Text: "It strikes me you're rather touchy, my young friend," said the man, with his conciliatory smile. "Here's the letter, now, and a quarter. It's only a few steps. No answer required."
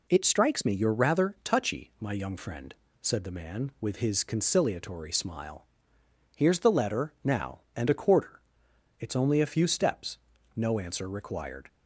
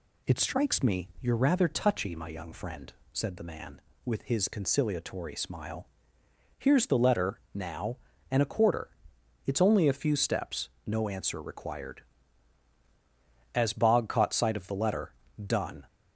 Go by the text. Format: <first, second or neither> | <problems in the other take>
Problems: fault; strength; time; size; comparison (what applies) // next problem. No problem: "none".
first | goes on to say "As Bog caught sight of the letter done"; strong; from 13.5 s on; 2.3 s long